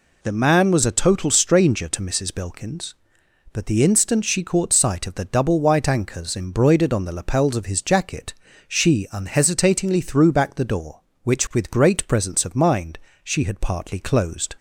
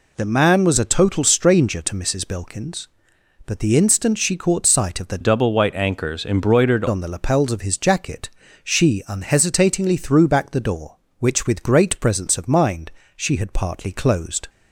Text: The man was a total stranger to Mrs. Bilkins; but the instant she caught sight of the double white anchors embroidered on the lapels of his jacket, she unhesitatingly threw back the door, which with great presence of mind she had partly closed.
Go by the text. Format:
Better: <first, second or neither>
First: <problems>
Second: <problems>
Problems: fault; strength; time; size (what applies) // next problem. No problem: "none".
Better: first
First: pauses between "mind" and "she"; slight; at 12.9 s; 0.26 s long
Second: changes voice from "double" to "embroidered"; from 5.2 to 6.8 s; 1.6 s long // pauses between "mind" and "she"; slight; at 12.8 s; 0.26 s long